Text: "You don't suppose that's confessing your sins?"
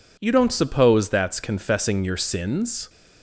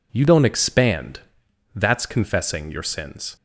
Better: first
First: none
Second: says "expand" for "suppose"; at 0.4 s

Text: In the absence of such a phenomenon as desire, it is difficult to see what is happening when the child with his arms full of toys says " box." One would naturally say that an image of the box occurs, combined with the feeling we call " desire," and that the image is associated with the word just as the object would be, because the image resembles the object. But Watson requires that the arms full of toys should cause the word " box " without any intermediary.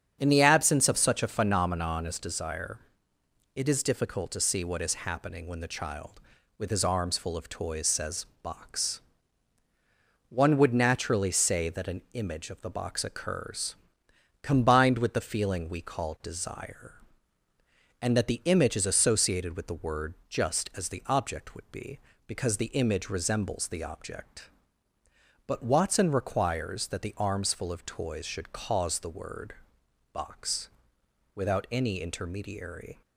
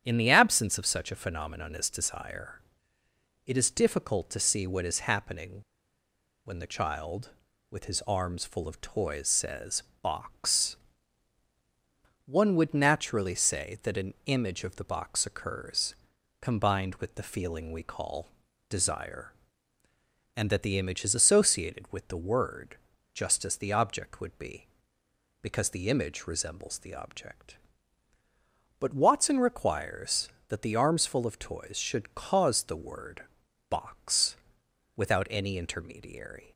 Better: first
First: starts louder than the rest; strong; until 1.2 s; 8 dB // pauses between "word" and "just"; slight; at 20.1 s; 0.16 s long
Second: starts louder than the rest; strong; until 1.0 s; 9.5 dB // pauses between "happening" and "when"; noticeable; at 5.5 s; 0.86 s long // pauses between "word" and "just"; at 22.7 s; 0.38 s long

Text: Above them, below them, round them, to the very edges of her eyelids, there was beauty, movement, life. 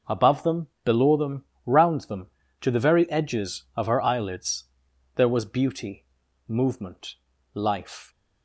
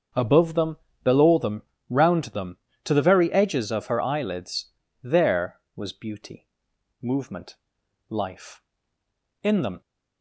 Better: first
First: none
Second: starts louder than the rest; until 1.4 s; 7 dB // goes on to say "In them"; slight; from 9.4 s on; 0.38 s long

